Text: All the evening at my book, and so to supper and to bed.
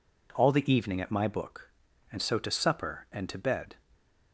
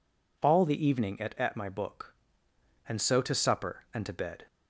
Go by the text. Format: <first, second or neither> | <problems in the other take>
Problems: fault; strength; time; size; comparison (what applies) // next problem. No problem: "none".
first | says "at" twice; at 1.3 s